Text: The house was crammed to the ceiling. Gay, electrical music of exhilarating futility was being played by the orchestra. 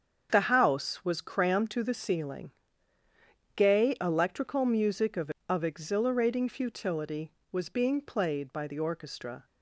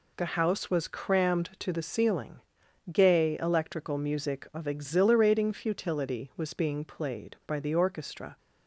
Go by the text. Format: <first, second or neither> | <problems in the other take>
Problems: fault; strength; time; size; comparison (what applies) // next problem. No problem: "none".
second | starts louder than the rest; strong; until 1.3 s; 7.5 dB // says "of" twice; at 5.4 s